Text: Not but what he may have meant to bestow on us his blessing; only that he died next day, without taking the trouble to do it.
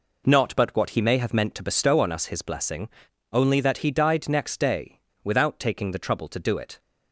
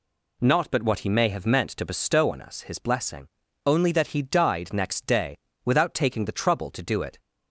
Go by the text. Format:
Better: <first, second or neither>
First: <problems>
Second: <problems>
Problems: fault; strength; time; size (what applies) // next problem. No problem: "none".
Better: neither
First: none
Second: none